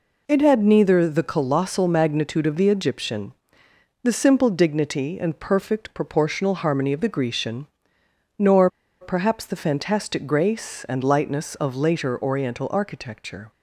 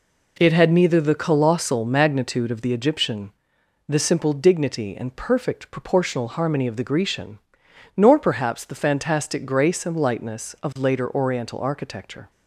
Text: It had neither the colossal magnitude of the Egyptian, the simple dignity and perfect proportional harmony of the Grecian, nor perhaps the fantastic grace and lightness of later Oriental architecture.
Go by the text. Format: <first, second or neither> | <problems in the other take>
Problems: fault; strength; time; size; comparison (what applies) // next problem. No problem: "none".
second | pauses between "nor" and "perhaps"; slight; at 8.6 s; 0.31 s long